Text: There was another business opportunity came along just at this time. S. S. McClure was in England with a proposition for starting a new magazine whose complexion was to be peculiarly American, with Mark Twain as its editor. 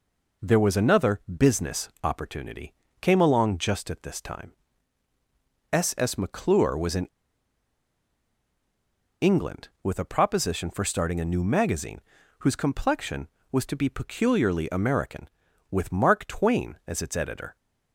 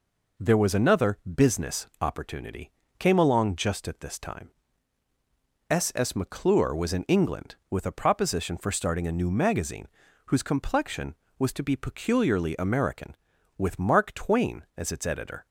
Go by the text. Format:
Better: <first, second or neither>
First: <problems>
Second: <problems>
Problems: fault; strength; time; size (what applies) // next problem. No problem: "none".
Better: second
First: pauses between "opportunity" and "came"; slight; at 2.7 s; 0.26 s long // pauses between "in" and "England"; strong; at 7.0 s; 2.1 s long // pauses between "magazine" and "whose"; at 11.9 s; 0.40 s long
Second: pauses between "opportunity" and "came"; slight; at 2.7 s; 0.26 s long // pauses between "magazine" and "whose"; at 9.8 s; 0.40 s long